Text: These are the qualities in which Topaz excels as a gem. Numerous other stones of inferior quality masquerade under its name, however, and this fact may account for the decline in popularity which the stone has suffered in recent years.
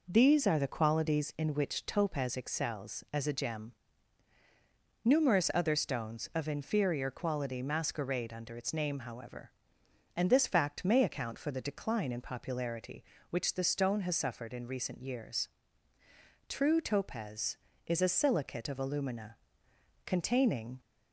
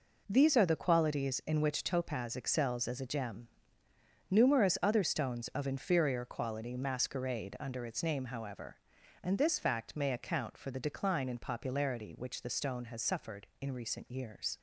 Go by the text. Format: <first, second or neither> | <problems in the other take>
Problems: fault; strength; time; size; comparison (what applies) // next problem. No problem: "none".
second | goes on to say "True Topaz is a silicate of alumina containing"; strong; from 16.4 s on; 4.3 s long